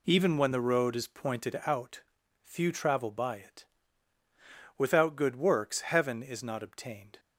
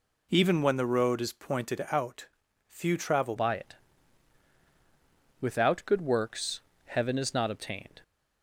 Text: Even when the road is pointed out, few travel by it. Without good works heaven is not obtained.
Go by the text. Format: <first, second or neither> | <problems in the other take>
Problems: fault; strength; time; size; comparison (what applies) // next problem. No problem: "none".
first | changes voice at "by"; from 3.3 s on; 4.7 s long // pauses between "works" and "heaven"; slight; at 6.5 s; 0.26 s long